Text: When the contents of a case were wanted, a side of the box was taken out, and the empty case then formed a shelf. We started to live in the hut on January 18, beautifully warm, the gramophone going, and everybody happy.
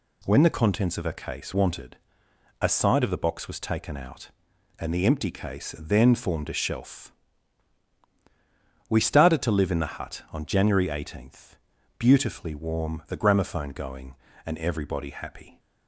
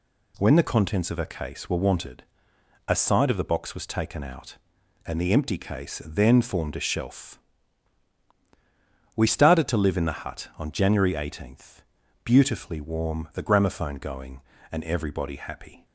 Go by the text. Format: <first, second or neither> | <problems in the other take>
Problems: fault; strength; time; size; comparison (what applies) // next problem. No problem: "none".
second | skips "were"; at 1.5 s